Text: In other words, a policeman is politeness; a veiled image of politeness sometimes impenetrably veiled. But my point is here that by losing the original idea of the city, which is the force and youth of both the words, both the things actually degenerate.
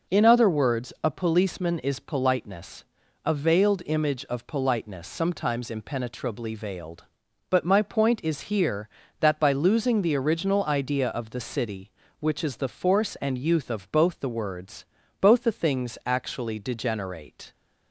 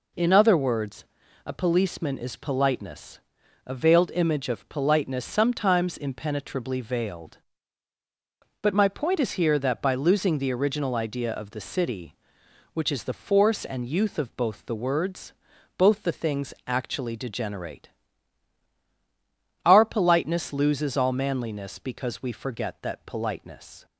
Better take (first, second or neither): first